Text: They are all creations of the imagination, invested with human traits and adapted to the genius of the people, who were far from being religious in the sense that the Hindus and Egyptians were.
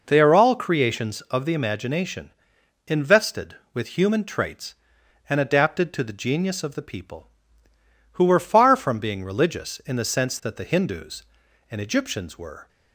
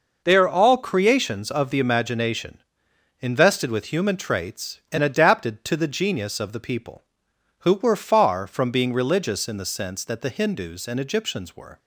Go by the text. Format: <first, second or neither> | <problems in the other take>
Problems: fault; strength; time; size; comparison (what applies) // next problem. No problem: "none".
neither | none